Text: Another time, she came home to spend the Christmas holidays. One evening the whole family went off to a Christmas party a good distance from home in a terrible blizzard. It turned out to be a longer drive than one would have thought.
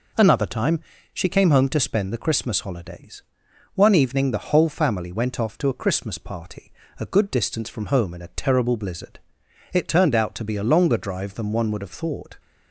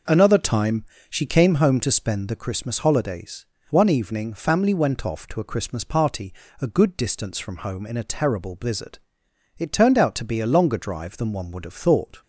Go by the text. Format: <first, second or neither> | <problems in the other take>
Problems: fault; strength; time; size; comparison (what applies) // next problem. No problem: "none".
first | skips "the whole"; at 4.3 s // pauses between "party" and "a"; slight; at 6.3 s; 0.30 s long; slight in the first